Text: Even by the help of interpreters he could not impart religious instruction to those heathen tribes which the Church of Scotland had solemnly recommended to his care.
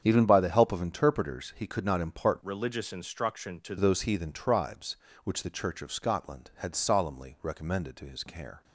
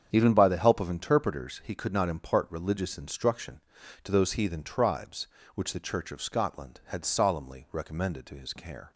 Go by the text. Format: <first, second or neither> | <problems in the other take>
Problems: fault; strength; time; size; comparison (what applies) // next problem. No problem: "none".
second | starts louder than the rest; strong; until 1.0 s; 8 dB; strong in the second // changes voice from "religious" to "to"; from 2.4 to 3.7 s; 1.3 s long